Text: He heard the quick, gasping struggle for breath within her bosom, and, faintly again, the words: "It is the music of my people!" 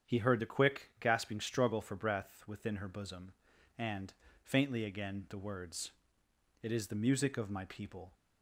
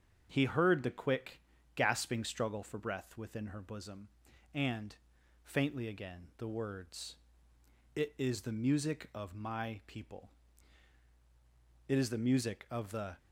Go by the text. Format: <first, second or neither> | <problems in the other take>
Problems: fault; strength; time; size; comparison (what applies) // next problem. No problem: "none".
first | starts louder than the rest; strong; until 1.3 s; 7.5 dB; strong in the first // goes on to say "It is the music of the"; noticeable; from 11.8 s on; 1.3 s long